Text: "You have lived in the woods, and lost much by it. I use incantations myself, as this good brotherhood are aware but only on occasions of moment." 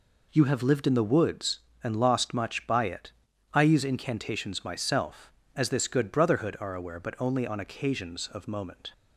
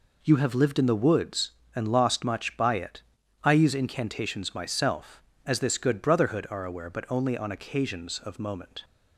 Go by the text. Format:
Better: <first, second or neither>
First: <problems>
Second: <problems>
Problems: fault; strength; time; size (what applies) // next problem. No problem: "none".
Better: neither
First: none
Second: none